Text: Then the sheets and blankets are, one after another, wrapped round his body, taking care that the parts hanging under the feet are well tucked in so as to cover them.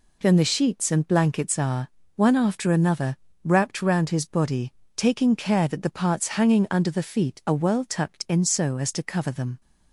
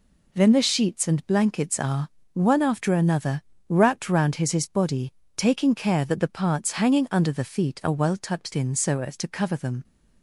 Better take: first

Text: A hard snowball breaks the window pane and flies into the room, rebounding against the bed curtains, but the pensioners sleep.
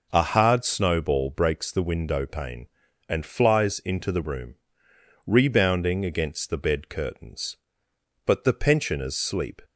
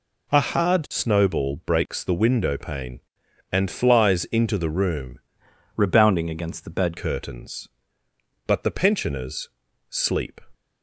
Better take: first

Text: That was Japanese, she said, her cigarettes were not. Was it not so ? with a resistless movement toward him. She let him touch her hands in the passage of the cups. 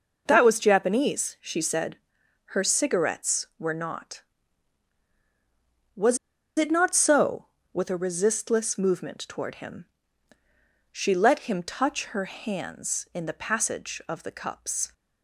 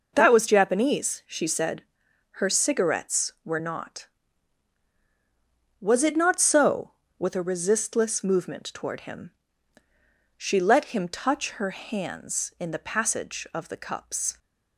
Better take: second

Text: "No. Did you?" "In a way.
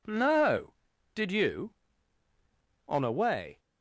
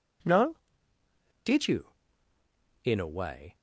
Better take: second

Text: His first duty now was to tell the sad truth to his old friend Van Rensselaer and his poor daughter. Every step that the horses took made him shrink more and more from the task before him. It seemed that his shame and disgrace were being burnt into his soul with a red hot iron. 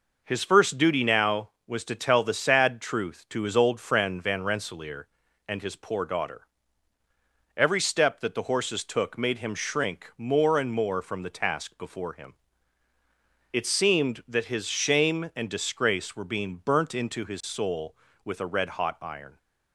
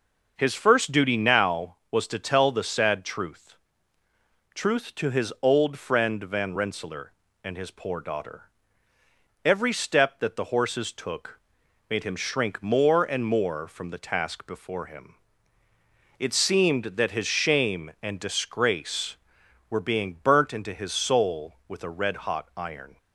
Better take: first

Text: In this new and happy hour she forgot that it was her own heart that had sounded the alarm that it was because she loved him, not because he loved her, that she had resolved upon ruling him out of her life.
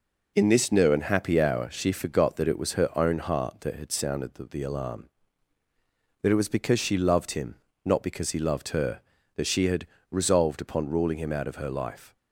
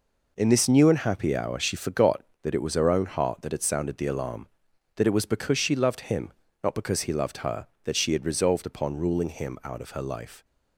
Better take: second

